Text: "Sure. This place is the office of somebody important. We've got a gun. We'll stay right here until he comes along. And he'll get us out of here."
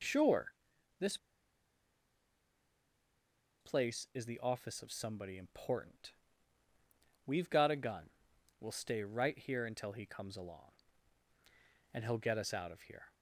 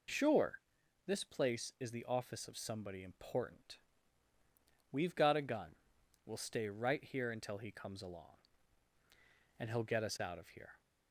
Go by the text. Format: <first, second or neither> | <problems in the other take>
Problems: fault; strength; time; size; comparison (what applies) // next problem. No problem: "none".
second | pauses between "This" and "place"; strong; at 1.1 s; 2.4 s long